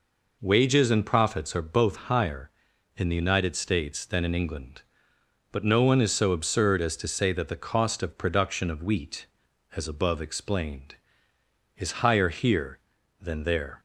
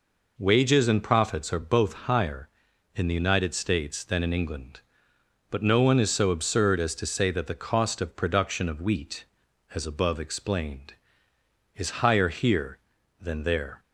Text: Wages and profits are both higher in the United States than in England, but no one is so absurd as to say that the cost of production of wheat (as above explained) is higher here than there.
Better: neither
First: none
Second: none

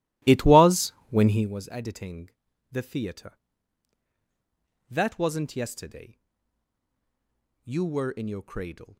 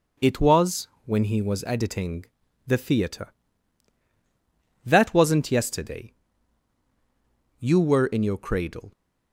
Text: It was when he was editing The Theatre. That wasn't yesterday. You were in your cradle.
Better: second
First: starts louder than the rest; strong; until 1.5 s; 16.5 dB // pauses between "was" and "when"; slight; at 0.9 s; 0.18 s long // pauses between "editing" and "The"; at 2.3 s; 0.40 s long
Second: pauses between "was" and "when"; slight; at 0.8 s; 0.18 s long // pauses between "editing" and "The"; at 2.2 s; 0.40 s long

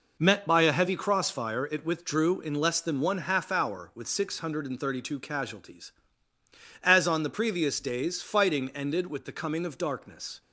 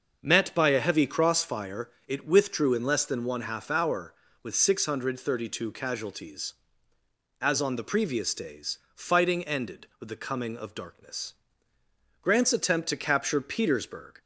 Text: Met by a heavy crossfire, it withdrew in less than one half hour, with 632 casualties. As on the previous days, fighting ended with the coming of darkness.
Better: first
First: none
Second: starts louder than the rest; until 1.2 s; 6 dB // goes on to say "Grant's attempt to capture Petersburg"; strong; from 12.2 s on; 2.0 s long

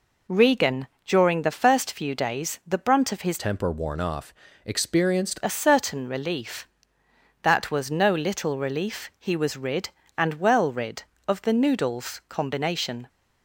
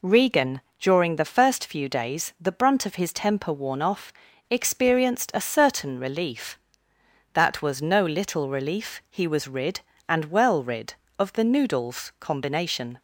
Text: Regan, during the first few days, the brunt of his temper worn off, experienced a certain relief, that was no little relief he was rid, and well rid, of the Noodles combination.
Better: second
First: changes voice from "temper" to "experienced"; from 3.3 to 5.3 s; 2.0 s long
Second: none

